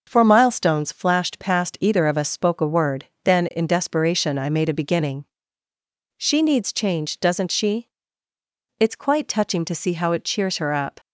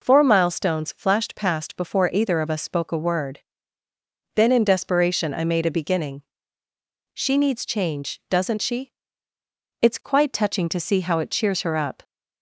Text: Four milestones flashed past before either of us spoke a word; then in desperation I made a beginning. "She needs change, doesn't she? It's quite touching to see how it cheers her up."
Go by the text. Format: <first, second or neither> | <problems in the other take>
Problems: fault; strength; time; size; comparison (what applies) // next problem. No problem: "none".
second | skips "before"; at 1.7 s